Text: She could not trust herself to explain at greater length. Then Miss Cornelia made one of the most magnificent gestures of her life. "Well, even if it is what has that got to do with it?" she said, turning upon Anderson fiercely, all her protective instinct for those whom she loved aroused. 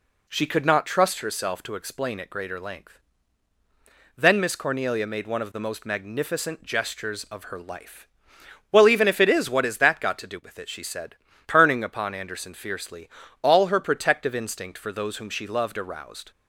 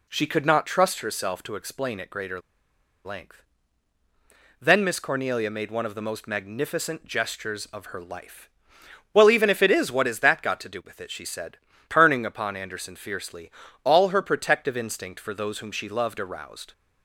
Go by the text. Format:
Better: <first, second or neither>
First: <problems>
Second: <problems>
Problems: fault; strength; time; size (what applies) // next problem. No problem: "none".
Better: first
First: none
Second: pauses between "greater" and "length"; noticeable; at 2.4 s; 0.64 s long